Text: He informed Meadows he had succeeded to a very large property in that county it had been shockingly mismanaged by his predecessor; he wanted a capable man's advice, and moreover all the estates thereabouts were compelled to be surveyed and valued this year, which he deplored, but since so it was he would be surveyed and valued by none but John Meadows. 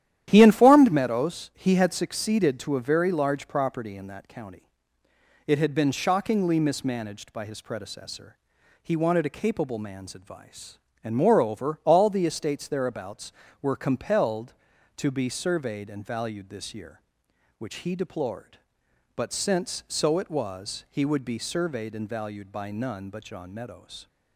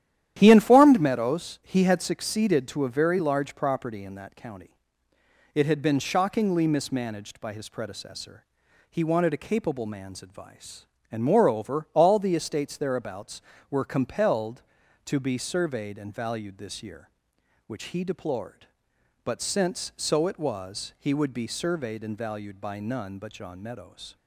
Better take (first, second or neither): neither